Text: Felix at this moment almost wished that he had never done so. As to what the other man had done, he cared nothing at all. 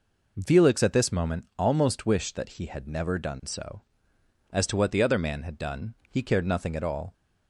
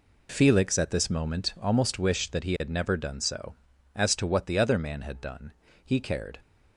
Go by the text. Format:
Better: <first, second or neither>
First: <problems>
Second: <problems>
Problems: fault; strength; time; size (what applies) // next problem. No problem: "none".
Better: first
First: none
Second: stops before "nothing at all"; at 6.3 s